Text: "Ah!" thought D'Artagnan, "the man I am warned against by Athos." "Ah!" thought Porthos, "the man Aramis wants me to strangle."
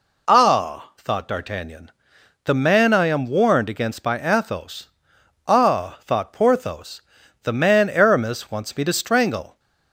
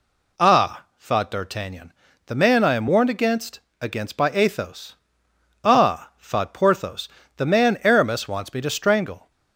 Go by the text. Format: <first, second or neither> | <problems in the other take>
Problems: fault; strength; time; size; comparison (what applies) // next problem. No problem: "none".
first | says "against" twice; at 3.7 s